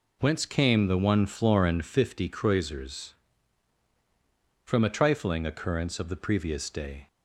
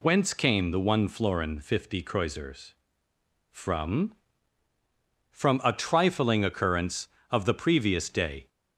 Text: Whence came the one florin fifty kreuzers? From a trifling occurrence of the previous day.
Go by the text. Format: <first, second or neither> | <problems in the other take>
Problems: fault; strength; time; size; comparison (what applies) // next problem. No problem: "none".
first | says "From" twice; at 5.3 s